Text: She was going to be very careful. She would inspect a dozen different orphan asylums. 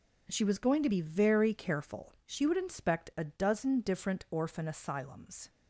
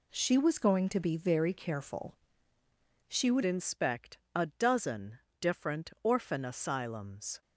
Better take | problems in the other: first | changes voice at "inspect"; from 3.4 s on; 4.0 s long // pauses between "inspect" and "a"; slight; at 4.1 s; 0.16 s long // pauses between "dozen" and "different"; slight; at 5.1 s; 0.24 s long

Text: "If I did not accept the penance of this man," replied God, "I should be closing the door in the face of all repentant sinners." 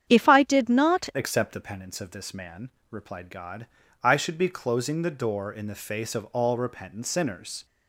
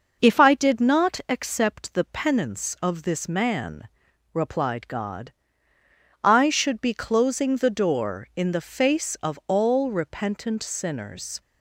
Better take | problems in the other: second | starts louder than the rest; strong; until 1.0 s; 9 dB // changes voice at "accept"; from 1.1 s on; 6.5 s long

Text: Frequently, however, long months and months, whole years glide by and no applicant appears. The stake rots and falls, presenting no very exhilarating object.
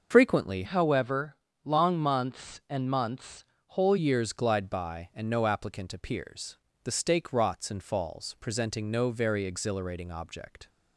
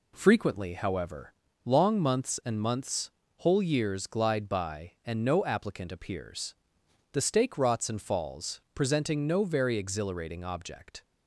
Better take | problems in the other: second | starts louder than the rest; until 1.1 s; 6 dB // changes voice from "however" to "whole"; from 0.6 to 3.9 s; 3.3 s long

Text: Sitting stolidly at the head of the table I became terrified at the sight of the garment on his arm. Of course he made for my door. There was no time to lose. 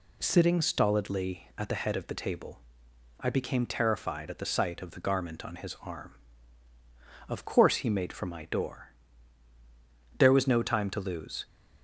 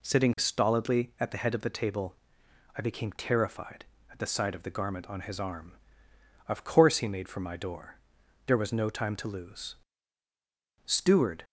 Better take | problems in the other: first | pauses between "table" and "I"; noticeable; at 2.1 s; 0.62 s long; noticeable in the first // goes on to say "Steward"; from 10.8 s on; 0.60 s long

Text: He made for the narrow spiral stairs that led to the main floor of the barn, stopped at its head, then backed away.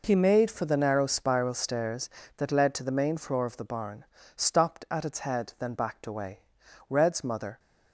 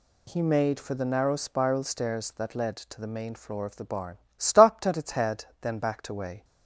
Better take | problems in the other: second | goes on to say "Red's mother"; noticeable; from 6.9 s on; 0.68 s long

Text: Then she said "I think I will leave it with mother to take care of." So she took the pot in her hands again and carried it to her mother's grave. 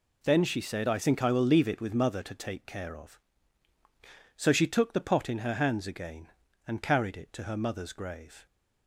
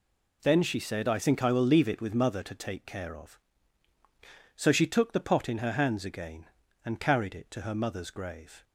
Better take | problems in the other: neither | none

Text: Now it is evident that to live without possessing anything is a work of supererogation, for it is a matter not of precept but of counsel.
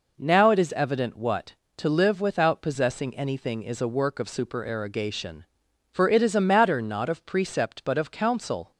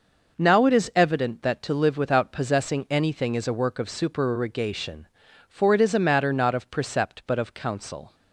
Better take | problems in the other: second | says "what" for "that"; at 1.1 s

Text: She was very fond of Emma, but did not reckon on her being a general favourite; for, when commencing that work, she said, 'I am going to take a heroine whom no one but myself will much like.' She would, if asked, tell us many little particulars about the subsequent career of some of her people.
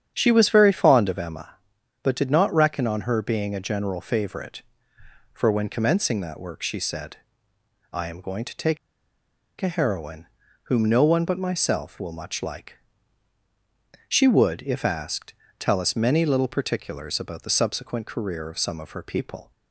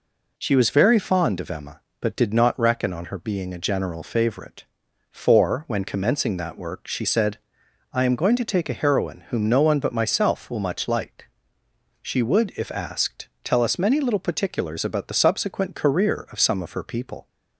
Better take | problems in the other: second | starts louder than the rest; strong; until 1.1 s; 8.5 dB // pauses between "take" and "a"; noticeable; at 8.7 s; 0.82 s long // pauses between "heroine" and "whom"; at 10.2 s; 0.42 s long

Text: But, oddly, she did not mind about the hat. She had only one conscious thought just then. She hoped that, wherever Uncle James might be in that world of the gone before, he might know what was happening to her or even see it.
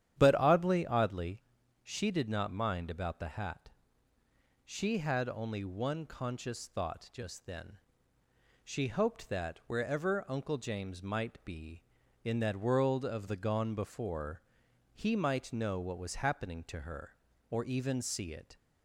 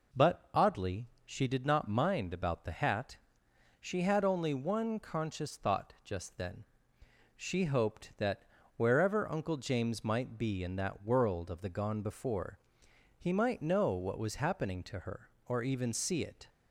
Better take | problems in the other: second | starts louder than the rest; strong; until 1.2 s; 10 dB // says "oddly" twice; at 0.8 s

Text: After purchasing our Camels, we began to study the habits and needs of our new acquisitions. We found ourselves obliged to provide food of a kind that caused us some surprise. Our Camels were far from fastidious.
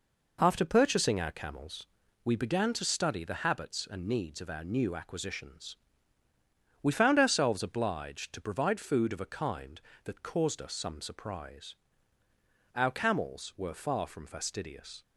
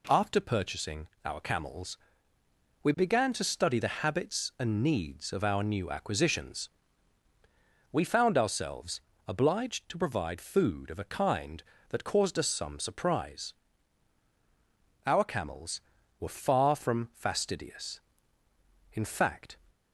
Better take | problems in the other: first | pauses between "purchasing" and "our"; slight; at 1.0 s; 0.16 s long // pauses between "ourselves" and "obliged"; slight; at 9.0 s; 0.24 s long // goes on to say "In fact"; noticeable; from 18.9 s on; 0.64 s long

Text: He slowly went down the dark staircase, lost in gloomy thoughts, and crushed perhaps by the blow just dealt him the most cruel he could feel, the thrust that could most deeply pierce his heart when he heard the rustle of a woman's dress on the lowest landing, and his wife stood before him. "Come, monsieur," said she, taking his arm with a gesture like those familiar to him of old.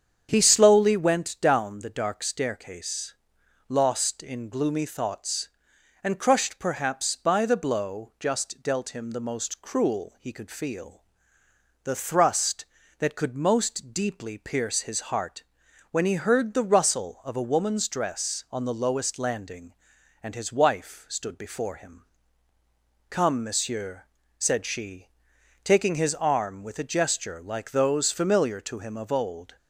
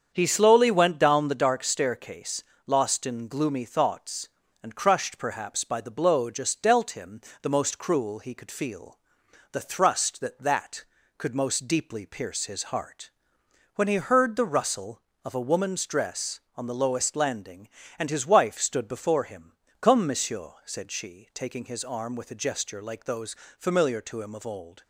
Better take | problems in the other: first | starts louder than the rest; strong; until 1.1 s; 7.5 dB; strong in the first // pauses between "him" and "the"; slight; at 7.2 s; 0.18 s long // says "that" twice; at 10.3 s // pauses between "heart" and "when"; noticeable; at 13.1 s; 0.64 s long; noticeable in the first // pauses between "those" and "familiar"; slight; at 23.3 s; 0.22 s long

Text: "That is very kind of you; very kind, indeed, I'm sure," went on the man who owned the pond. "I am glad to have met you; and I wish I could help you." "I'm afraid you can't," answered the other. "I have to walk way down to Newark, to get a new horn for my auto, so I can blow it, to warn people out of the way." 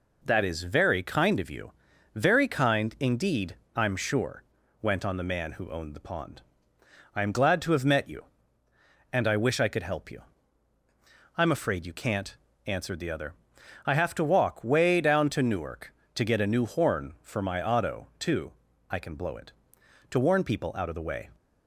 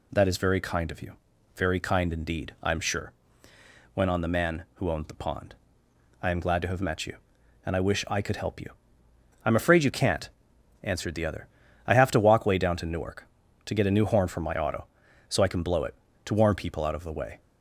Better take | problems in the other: second | says "too" for "so"; at 18.2 s

